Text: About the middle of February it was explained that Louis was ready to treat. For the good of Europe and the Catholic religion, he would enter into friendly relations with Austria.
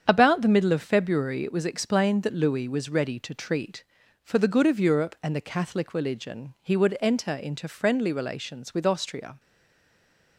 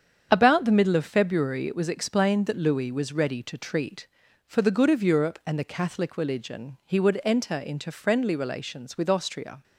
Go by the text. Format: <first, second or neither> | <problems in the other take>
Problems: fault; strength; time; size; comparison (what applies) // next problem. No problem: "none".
second | starts louder than the rest; strong; until 1.0 s; 8 dB; strong in the second // stays silent after the last word; from 9.3 s on; 1.0 s long